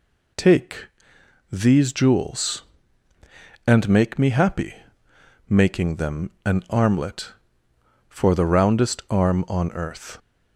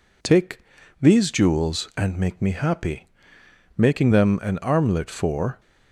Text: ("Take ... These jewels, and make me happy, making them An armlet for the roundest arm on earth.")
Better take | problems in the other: first | stops before "the roundest arm on earth"; at 5.5 s

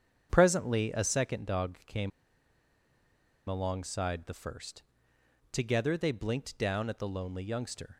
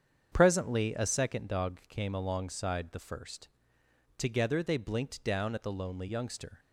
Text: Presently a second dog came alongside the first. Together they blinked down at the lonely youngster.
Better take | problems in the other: second | starts louder than the rest; strong; until 1.3 s; 8 dB; strong in the second // pauses between "came" and "alongside"; strong; at 2.1 s; 1.3 s long

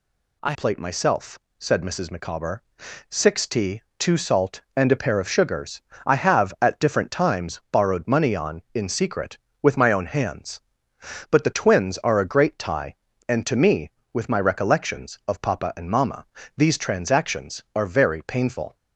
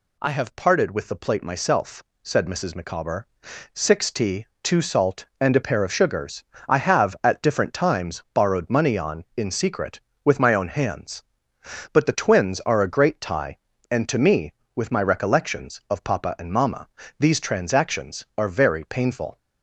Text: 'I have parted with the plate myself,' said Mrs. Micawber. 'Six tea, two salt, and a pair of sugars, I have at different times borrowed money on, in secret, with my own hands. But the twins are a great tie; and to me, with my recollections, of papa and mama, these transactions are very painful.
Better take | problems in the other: second | skips "have parted with the"; at 0.5 s

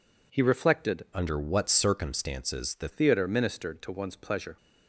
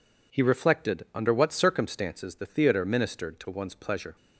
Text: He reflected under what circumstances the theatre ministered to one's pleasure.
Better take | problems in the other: second | changes voice from "under" to "the"; from 1.1 to 2.8 s; 1.7 s long

